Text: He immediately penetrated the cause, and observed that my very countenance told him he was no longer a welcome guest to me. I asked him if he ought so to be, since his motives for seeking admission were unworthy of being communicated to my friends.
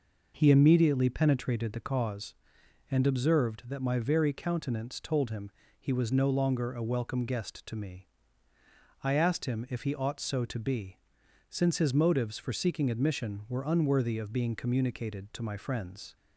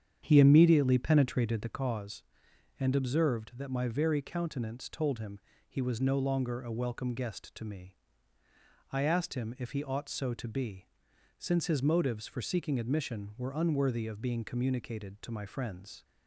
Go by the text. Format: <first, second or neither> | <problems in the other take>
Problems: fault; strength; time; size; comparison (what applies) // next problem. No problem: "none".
first | starts louder than the rest; strong; until 1.8 s; 8.5 dB // pauses between "him" and "he"; slight; at 5.3 s; 0.30 s long; slight in the first